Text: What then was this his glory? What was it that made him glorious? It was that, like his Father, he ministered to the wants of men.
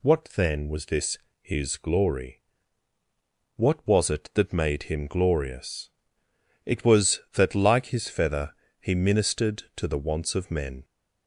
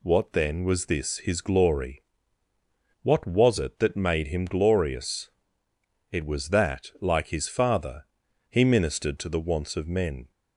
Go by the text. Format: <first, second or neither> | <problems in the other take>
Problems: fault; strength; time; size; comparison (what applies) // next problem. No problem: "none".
second | pauses between "this" and "his"; slight; at 1.1 s; 0.24 s long // says "Feather" for "Father"; at 8.0 s